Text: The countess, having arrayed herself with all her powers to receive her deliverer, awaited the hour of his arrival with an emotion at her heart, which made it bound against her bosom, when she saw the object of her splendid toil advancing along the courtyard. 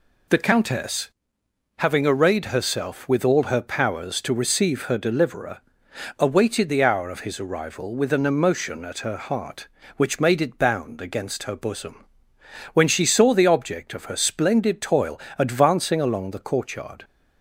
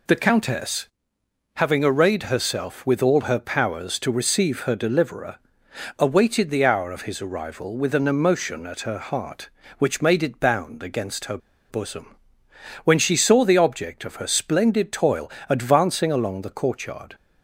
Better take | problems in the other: first | pauses between "her" and "bosom"; slight; at 11.3 s; 0.32 s long // pauses between "toil" and "advancing"; slight; at 15.3 s; 0.18 s long; slight in the first

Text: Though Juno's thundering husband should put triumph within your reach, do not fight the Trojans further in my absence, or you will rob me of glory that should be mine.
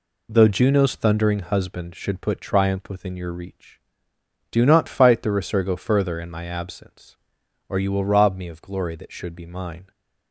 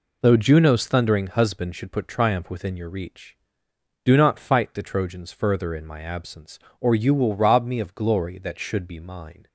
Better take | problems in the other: second | says "Resurgo" for "Trojans"; at 5.3 s

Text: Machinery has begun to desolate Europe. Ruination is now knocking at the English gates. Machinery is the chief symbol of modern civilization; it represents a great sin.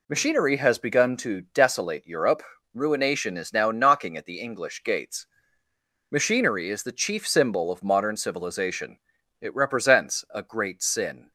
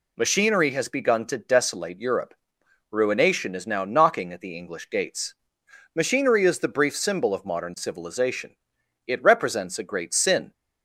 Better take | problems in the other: first | says "brief" for "chief"; at 6.6 s

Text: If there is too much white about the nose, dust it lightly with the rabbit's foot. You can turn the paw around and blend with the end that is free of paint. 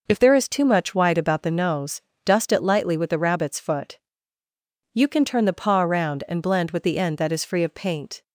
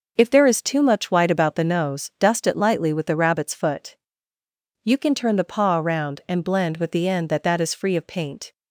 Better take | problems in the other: first | says "that" twice; at 7.4 s

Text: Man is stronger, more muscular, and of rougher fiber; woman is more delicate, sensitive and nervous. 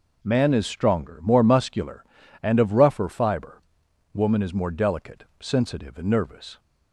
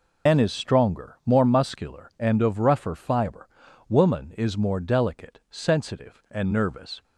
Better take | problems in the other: first | loses the start of "Man"; at 0.2 s; 145 ms

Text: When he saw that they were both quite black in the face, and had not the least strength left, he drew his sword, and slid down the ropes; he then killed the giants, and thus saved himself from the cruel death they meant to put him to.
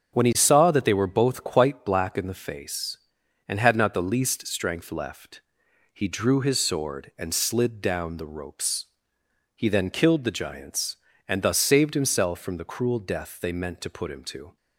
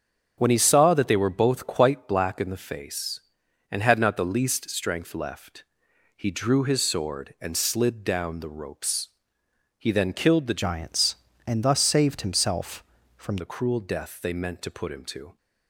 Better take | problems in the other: first | starts louder than the rest; until 1.3 s; 7 dB; strong in the first // changes voice from "giants" to "from"; from 10.6 to 13.3 s; 2.7 s long

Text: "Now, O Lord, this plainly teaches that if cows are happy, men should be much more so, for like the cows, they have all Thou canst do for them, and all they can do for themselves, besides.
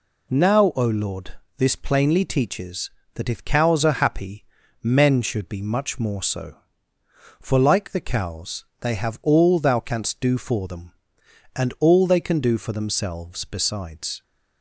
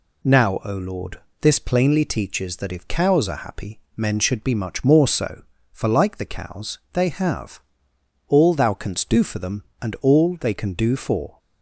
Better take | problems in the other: first | pauses between "have" and "all"; noticeable; at 7.6 s; 0.68 s long // stops before "themselves besides"; at 11.3 s

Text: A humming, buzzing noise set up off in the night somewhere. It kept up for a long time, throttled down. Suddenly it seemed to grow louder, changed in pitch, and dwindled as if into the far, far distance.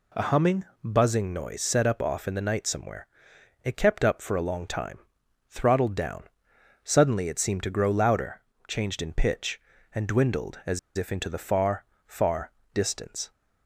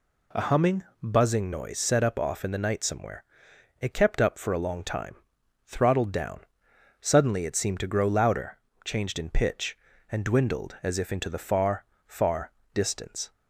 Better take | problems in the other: second | pauses between "as" and "if"; slight; at 10.7 s; 0.19 s long // pauses between "far" and "distance"; slight; at 12.5 s; 0.24 s long; slight in the second

